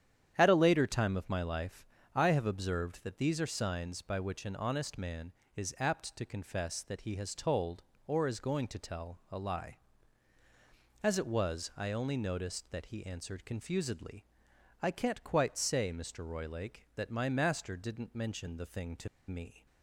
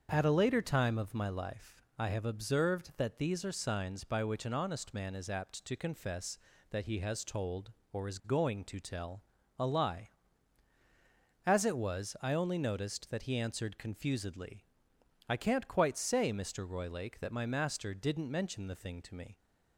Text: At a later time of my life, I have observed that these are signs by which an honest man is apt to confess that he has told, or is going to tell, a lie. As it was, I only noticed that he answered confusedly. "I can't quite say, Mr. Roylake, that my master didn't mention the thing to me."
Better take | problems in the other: second | starts louder than the rest; strong; until 1.3 s; 9.5 dB; also in the second // pauses between "to" and "me"; slight; at 19.0 s; 0.21 s long

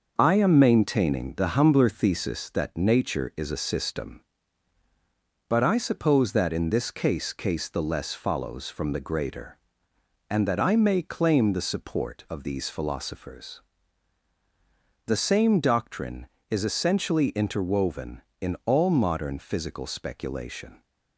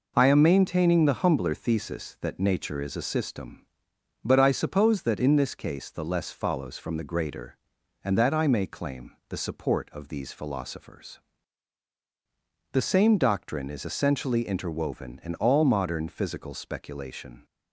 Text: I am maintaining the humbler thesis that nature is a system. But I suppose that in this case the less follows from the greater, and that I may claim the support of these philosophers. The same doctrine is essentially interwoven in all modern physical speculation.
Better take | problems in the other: second | starts louder than the rest; until 1.1 s; 6.5 dB // says "case" twice; at 7.3 s

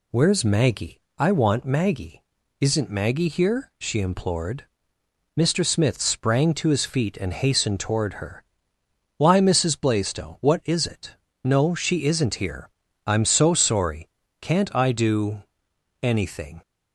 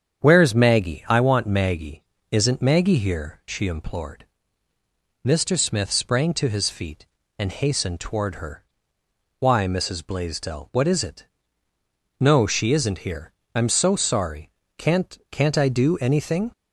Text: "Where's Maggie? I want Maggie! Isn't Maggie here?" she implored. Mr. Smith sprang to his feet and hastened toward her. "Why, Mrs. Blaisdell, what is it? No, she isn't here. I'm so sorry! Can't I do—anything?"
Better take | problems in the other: first | starts louder than the rest; strong; until 1.2 s; 8 dB // says "Can't" twice; at 15.3 s

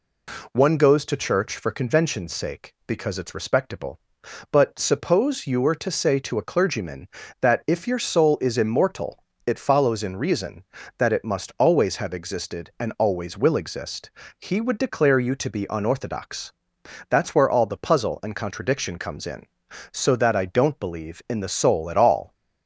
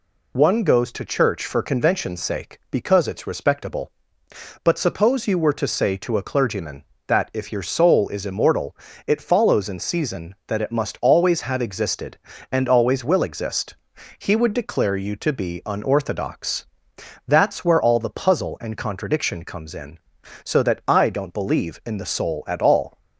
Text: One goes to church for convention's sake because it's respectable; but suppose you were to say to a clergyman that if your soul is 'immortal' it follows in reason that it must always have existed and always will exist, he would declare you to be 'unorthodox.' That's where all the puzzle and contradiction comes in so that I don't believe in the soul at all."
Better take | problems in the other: first | pauses between "immortal" and "it"; slight; at 8.7 s; 0.30 s long; slight in the first // says "season" for "reason"; at 9.7 s

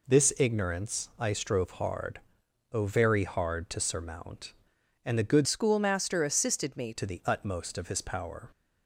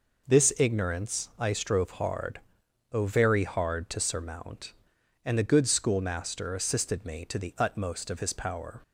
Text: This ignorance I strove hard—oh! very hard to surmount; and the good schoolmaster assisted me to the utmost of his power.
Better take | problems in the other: second | changes voice from "schoolmaster" to "me"; from 5.4 to 6.9 s; 1.5 s long

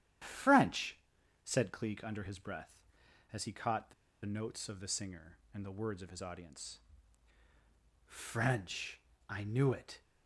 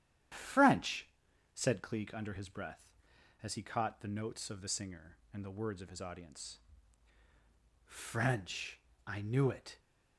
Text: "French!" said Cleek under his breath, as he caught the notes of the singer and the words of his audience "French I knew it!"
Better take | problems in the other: second | starts louder than the rest; strong; until 1.6 s; 10.5 dB; strong in the second // pauses between "the" and "notes"; slight; at 3.9 s; 0.31 s long // pauses between "audience" and "French"; at 6.8 s; 1.2 s long; also in the second // pauses between "French" and "I"; slight; at 8.9 s; 0.30 s long; slight in the second

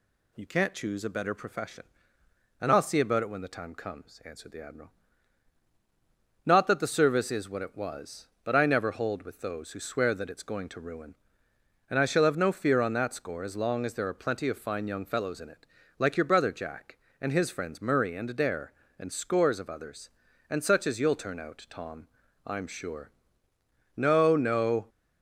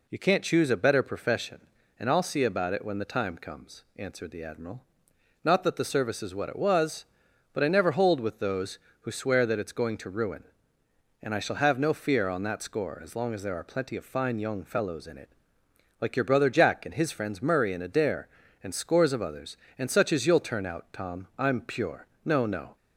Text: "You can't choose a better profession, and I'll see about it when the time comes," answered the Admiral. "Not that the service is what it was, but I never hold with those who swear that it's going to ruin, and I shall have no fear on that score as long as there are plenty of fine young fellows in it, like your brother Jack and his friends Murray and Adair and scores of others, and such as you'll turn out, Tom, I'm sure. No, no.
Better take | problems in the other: first | says "pure" for "sure"; at 21.6 s

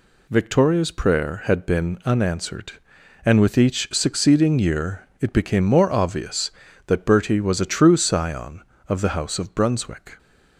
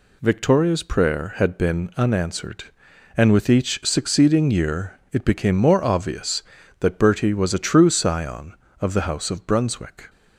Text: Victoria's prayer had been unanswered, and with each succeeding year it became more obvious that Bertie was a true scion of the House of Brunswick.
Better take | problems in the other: neither | pauses between "year" and "it"; slight; the same in both

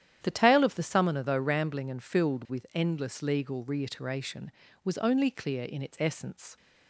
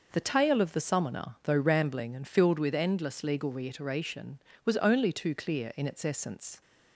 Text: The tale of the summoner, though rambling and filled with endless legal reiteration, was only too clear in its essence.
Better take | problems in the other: second | starts louder than the rest; strong; until 1.2 s; 10.5 dB // skips "too"; at 5.2 s

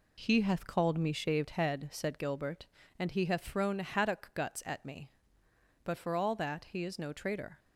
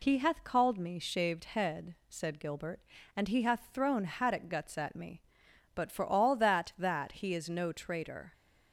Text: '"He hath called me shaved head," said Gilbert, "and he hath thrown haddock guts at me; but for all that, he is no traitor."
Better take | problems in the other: first | says "that" twice; at 6.7 s

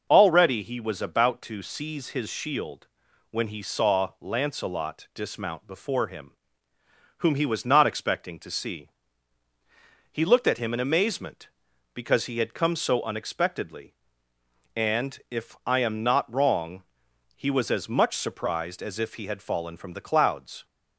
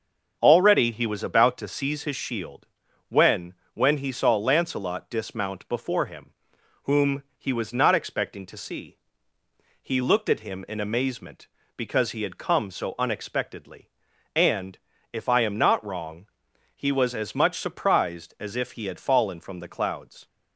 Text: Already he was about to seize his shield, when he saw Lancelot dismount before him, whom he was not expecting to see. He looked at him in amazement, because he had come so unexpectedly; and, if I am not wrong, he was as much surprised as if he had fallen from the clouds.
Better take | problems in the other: first | starts louder than the rest; until 1.4 s; 7 dB // says "when" twice; at 3.7 s

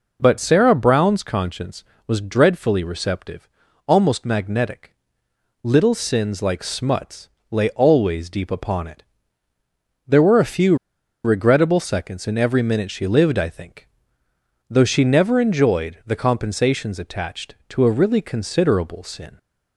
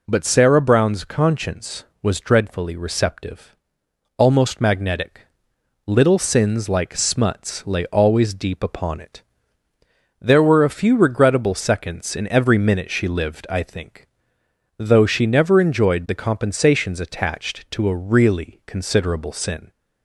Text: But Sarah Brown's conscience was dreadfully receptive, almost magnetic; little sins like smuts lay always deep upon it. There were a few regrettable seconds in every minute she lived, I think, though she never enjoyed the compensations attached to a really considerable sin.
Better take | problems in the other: second | pauses between "smuts" and "lay"; slight; at 7.2 s; 0.20 s long // pauses between "few" and "regrettable"; noticeable; at 10.7 s; 0.49 s long

